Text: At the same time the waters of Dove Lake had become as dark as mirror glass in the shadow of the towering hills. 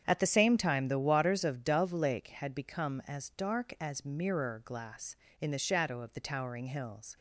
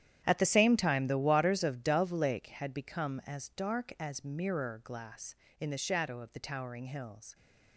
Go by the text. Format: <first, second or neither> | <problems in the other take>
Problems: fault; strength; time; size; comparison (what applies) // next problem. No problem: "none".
first | gets quieter; strong; throughout; 15 dB // starts louder than the rest; strong; until 1.2 s; 10 dB; strong in the first